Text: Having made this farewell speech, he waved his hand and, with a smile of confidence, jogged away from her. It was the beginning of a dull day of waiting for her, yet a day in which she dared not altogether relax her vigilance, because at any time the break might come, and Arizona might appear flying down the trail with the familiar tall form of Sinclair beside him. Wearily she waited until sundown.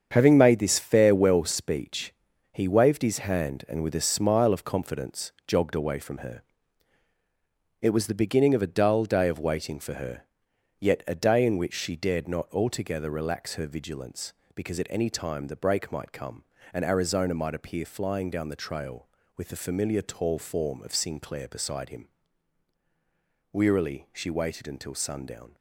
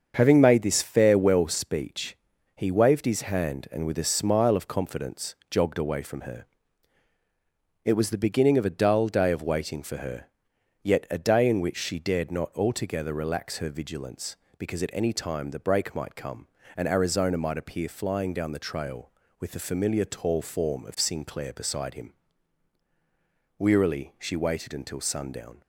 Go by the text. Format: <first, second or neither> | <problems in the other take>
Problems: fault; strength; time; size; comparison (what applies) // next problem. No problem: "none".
second | gets quieter; strong; throughout; 9 dB // starts louder than the rest; strong; until 1.1 s; 7.5 dB; also in the second